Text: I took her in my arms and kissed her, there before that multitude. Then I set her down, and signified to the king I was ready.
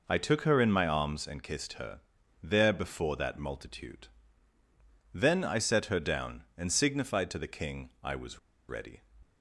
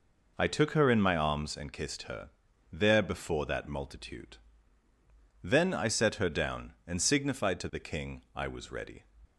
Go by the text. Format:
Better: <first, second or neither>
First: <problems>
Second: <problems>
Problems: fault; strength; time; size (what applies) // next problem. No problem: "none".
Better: second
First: pauses between "was" and "ready"; slight; at 8.3 s; 0.30 s long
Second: none